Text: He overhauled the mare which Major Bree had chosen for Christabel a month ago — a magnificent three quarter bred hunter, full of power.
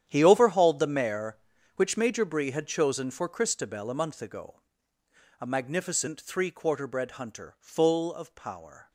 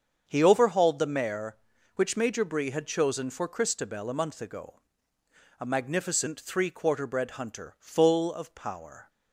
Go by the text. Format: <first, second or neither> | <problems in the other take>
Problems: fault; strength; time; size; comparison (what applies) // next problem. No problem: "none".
second | gets quieter; strong; throughout; 14.5 dB // starts louder than the rest; strong; until 1.0 s; 10 dB; strong in the second